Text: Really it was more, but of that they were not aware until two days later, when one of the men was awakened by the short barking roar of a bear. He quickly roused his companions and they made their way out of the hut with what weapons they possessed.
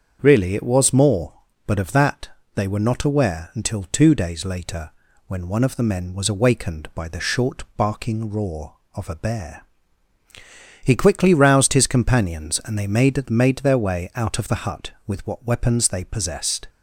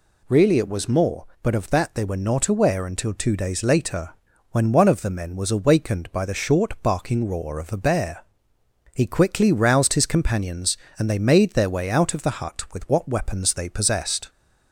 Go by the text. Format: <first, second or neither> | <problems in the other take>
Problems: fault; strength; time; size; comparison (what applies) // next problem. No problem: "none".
second | starts louder than the rest; strong; until 1.2 s; 7.5 dB // pauses between "that" and "they"; slight; at 2.2 s; 0.26 s long // says "made" twice; at 13.3 s